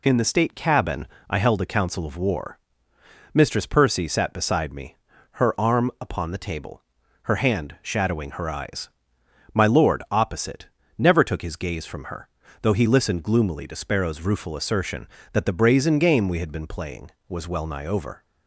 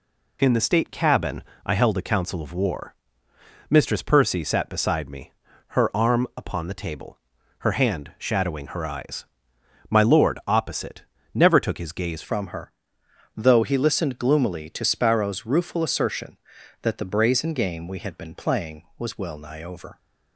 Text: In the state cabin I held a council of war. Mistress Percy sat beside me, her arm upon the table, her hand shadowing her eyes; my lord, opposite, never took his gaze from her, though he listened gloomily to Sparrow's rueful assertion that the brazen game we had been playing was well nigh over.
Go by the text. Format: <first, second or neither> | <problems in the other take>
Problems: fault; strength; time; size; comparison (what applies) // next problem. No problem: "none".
first | pauses between "cabin" and "I"; slight; at 1.4 s; 0.24 s long; slight in the first // changes voice at "from"; from 12.2 s on; 7.7 s long